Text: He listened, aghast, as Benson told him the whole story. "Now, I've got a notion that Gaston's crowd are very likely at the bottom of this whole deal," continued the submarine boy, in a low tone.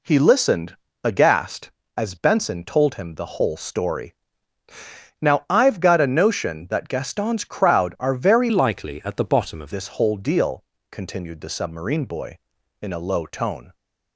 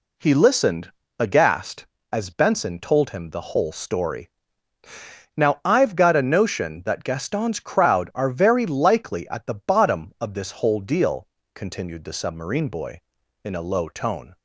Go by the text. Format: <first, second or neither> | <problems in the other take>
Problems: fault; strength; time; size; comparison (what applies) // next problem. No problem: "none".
second | changes voice from "likely" to "of"; from 8.5 to 9.7 s; 1.2 s long